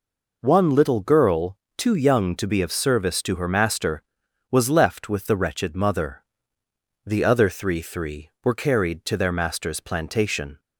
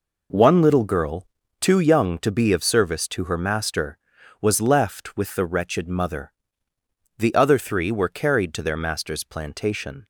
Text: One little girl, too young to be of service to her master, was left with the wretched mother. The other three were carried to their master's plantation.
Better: second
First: says "three" twice; at 7.8 s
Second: none

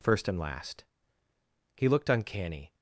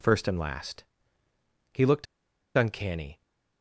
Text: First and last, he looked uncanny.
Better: first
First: none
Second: pauses between "looked" and "uncanny"; noticeable; at 2.0 s; 0.51 s long

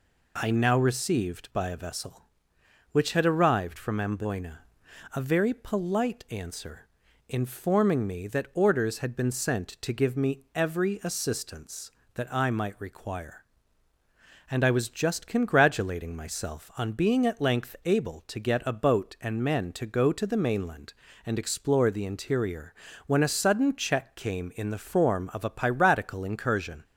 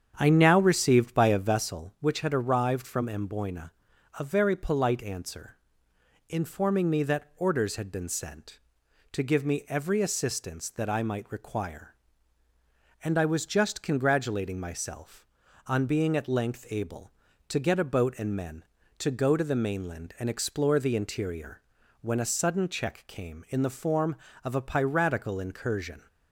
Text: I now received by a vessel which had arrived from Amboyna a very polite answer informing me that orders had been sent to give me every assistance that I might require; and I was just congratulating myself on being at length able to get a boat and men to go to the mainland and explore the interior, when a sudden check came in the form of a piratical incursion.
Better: first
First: pauses between "Amboyna" and "a"; noticeable; at 4.6 s; 0.48 s long // pauses between "answer" and "informing"; at 6.8 s; 0.38 s long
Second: starts louder than the rest; strong; until 1.8 s; 8 dB // pauses between "Amboyna" and "a"; at 3.7 s; 0.44 s long // pauses between "answer" and "informing"; noticeable; at 5.5 s; 0.72 s long

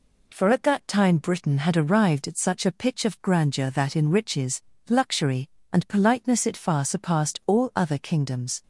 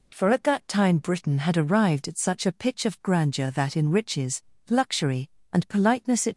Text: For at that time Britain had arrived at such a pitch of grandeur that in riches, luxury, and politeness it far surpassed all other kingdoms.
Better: first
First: none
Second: stops before "far surpassed all other kingdoms"; at 6.3 s

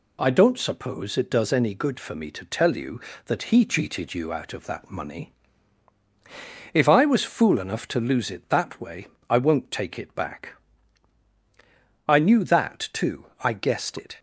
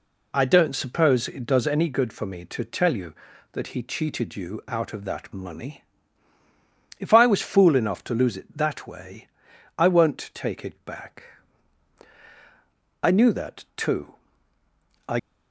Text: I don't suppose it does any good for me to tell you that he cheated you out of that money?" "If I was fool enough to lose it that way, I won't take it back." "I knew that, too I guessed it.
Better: first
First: none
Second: pauses between "too" and "I"; noticeable; at 14.1 s; 0.90 s long // stops before "guessed it"; at 15.1 s

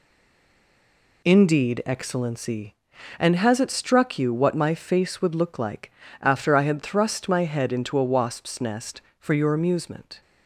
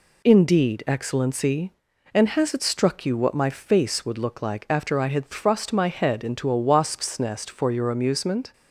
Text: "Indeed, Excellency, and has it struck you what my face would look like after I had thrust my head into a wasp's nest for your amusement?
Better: second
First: stays silent before the first word; noticeable; until 1.2 s; 1.2 s long // pauses between "like" and "after"; slight; at 5.9 s; 0.28 s long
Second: none

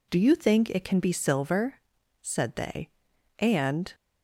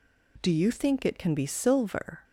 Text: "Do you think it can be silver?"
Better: second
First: goes on to say "said they and"; strong; from 2.2 s on; 1.7 s long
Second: none

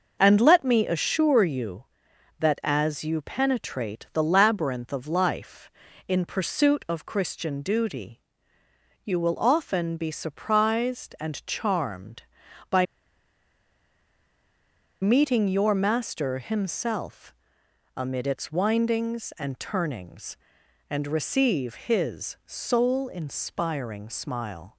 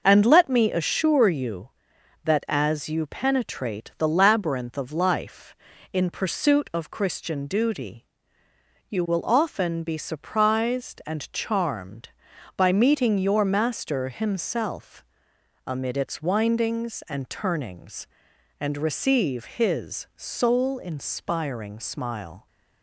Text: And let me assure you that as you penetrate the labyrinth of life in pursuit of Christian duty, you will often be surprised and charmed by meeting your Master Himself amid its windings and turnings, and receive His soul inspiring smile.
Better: second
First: pauses between "by" and "meeting"; strong; at 12.8 s; 2.1 s long // pauses between "Himself" and "amid"; noticeable; at 17.3 s; 0.64 s long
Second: pauses between "Himself" and "amid"; noticeable; at 15.0 s; 0.64 s long

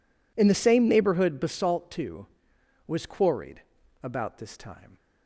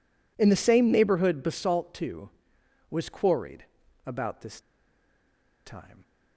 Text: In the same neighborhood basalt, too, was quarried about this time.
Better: first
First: pauses between "quarried" and "about"; at 3.6 s; 0.40 s long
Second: pauses between "quarried" and "about"; at 3.6 s; 0.40 s long // pauses between "this" and "time"; at 4.5 s; 1.0 s long

